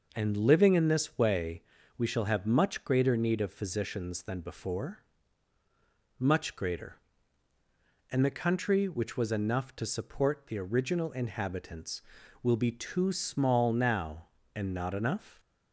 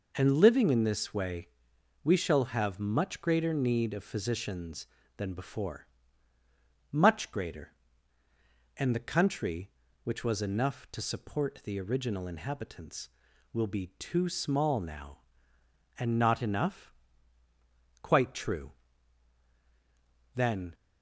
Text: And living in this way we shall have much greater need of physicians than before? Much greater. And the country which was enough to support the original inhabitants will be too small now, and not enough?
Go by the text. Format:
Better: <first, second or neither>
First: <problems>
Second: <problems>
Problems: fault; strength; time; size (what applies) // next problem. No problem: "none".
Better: first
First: pauses between "way" and "we"; slight; at 1.6 s; 0.36 s long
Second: pauses between "way" and "we"; noticeable; at 1.4 s; 0.56 s long // goes on to say "Quite true Then"; strong; from 18.0 s on; 2.7 s long